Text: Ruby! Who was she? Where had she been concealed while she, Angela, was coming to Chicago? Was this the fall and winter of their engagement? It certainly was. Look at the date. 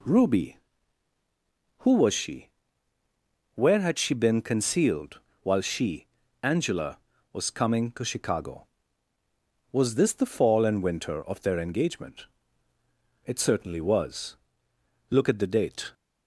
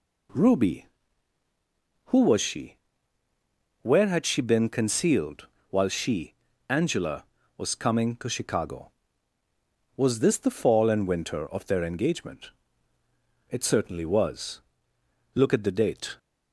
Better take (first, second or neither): neither